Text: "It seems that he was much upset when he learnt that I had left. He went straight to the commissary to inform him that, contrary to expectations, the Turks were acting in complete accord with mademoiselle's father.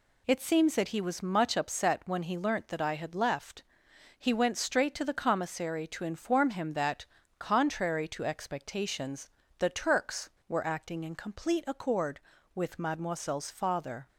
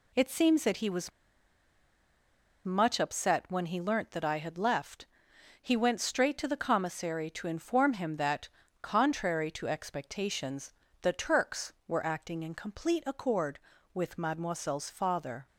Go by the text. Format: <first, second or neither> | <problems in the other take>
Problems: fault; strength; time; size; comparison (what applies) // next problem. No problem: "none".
first | pauses between "was" and "much"; strong; at 1.1 s; 1.5 s long